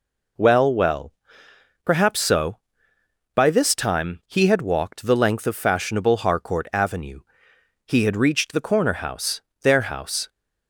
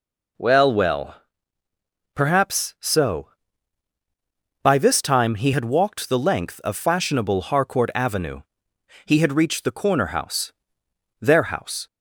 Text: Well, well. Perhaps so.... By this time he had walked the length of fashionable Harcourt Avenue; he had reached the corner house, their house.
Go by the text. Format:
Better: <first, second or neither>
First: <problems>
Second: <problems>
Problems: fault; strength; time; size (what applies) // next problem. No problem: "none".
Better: neither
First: none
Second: none